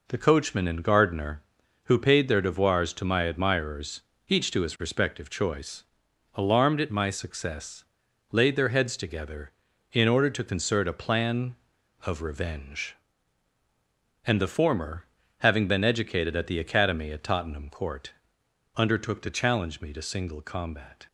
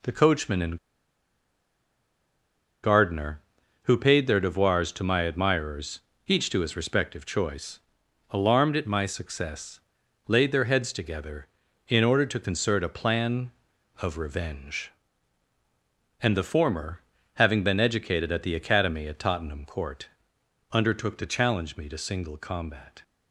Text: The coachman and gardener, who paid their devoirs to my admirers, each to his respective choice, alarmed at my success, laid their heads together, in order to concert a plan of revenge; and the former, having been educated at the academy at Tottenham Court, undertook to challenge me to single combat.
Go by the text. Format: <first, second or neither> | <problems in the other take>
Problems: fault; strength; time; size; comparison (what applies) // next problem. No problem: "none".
first | pauses between "and" and "gardener"; strong; at 0.7 s; 2.0 s long